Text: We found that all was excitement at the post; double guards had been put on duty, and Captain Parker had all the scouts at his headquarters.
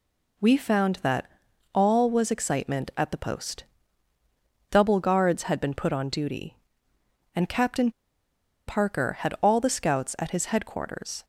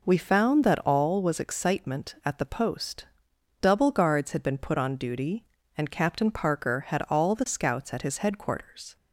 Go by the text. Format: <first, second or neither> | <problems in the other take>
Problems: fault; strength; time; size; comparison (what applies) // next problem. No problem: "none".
second | pauses between "that" and "all"; noticeable; at 1.2 s; 0.48 s long // pauses between "Captain" and "Parker"; noticeable; at 7.8 s; 0.77 s long